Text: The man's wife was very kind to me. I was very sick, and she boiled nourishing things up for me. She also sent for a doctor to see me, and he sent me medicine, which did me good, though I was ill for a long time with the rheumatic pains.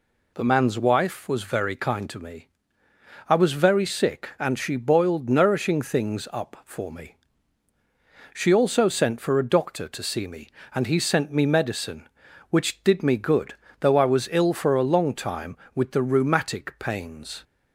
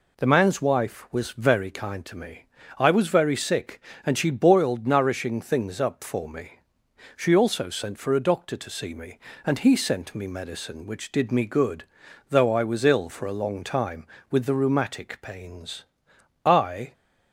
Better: first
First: none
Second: goes on to say "I"; slight; from 16.4 s on; 0.48 s long

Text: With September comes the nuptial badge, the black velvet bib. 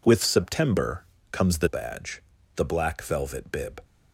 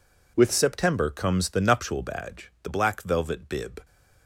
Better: second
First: pauses between "September" and "comes"; slight; at 1.0 s; 0.26 s long // skips "nuptial"; at 1.6 s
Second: none

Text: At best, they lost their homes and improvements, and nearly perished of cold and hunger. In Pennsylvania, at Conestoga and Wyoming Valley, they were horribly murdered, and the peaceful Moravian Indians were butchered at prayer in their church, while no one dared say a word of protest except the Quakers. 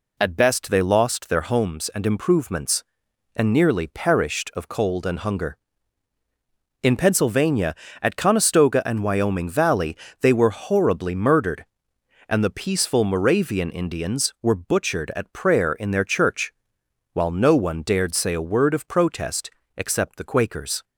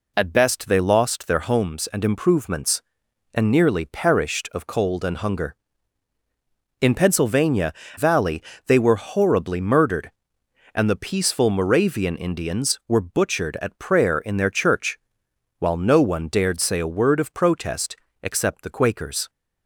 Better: first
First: pauses between "protest" and "except"; slight; at 19.4 s; 0.28 s long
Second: skips "at Conestoga and Wyoming"; at 7.8 s // pauses between "protest" and "except"; slight; at 17.9 s; 0.28 s long

